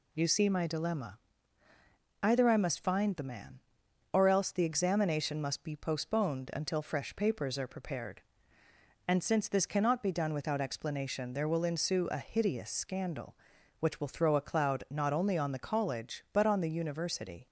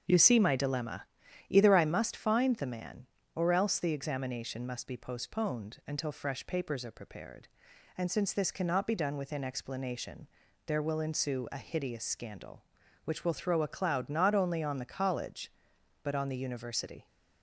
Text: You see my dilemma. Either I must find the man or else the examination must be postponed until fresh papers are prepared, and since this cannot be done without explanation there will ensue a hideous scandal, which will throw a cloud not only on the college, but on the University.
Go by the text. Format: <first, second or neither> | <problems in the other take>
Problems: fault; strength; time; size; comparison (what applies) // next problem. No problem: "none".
first | starts louder than the rest; until 1.5 s; 7 dB // says "within" for "without"; at 9.1 s // pauses between "explanation" and "there"; at 10.2 s; 0.40 s long